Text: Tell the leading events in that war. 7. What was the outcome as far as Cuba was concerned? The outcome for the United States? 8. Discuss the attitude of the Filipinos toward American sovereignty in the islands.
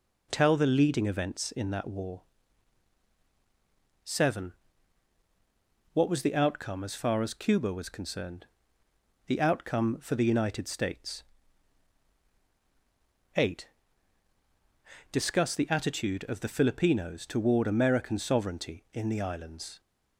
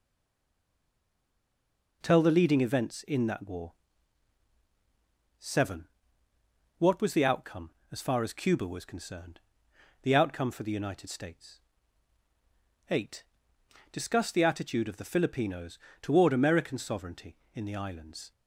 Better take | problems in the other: first | stays silent before the first word; noticeable; until 2.0 s; 2.0 s long // pauses between "Filipinos" and "toward"; slight; at 15.7 s; 0.24 s long

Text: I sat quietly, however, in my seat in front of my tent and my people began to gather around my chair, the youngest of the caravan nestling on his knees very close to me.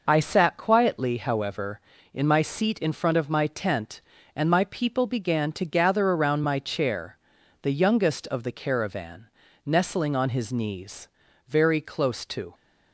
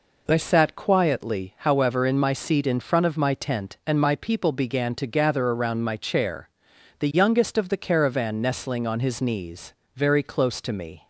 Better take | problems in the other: second | pauses between "caravan" and "nestling"; slight; at 9.2 s; 0.36 s long // pauses between "knees" and "very"; at 11.0 s; 0.40 s long; slight in the second // stops before "me"; at 12.5 s

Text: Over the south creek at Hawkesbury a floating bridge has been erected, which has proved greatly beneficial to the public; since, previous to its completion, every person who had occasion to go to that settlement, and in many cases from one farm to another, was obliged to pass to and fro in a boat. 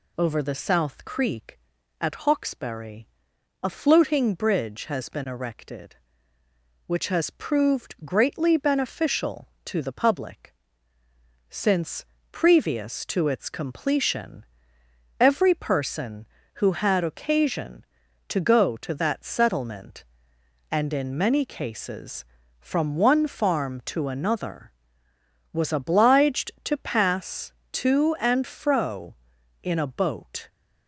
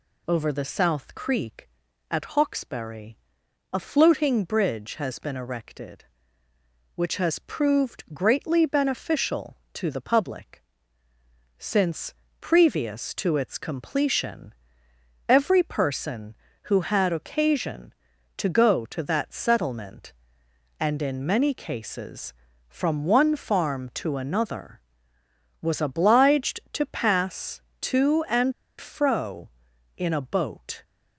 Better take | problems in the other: first | pauses between "Hawkesbury" and "a"; noticeable; at 3.1 s; 0.52 s long; noticeable in the first // pauses between "and" and "fro"; slight; at 28.5 s; 0.27 s long

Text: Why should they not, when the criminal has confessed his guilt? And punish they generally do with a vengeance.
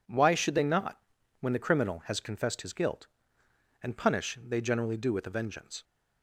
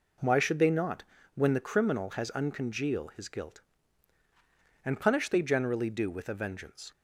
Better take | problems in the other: first | says "uncongeal" for "confessed"; at 2.3 s

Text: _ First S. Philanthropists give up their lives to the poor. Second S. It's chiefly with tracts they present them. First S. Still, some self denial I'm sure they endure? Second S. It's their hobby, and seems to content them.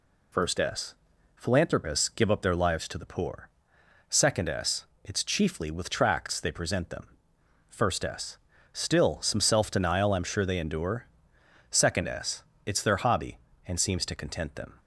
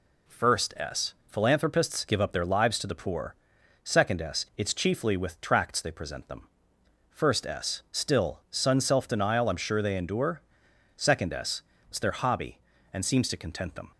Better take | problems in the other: first | says "sun" for "some"; at 8.5 s

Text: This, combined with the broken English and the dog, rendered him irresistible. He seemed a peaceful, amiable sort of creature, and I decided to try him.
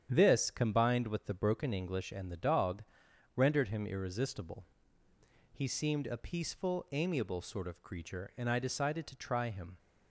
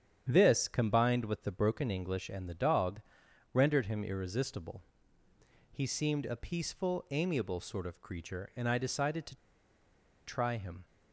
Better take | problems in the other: first | starts louder than the rest; strong; until 1.3 s; 9 dB; strong in the first // pauses between "to" and "try"; noticeable; at 9.3 s; 0.90 s long

